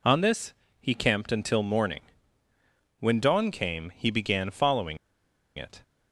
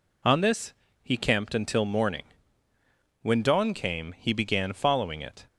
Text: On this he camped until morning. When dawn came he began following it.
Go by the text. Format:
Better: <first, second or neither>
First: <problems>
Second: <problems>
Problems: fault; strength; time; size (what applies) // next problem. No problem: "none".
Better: second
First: pauses between "this" and "he"; slight; at 0.5 s; 0.28 s long // pauses between "following" and "it"; noticeable; at 4.9 s; 0.60 s long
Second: pauses between "this" and "he"; slight; at 0.7 s; 0.30 s long